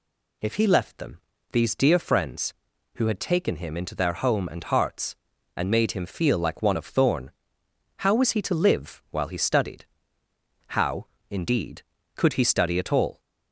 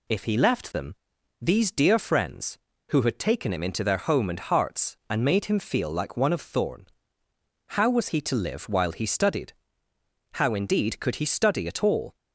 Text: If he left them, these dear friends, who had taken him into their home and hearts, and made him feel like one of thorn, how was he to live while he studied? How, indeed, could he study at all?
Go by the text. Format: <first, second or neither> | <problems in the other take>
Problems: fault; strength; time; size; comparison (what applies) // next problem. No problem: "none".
neither | none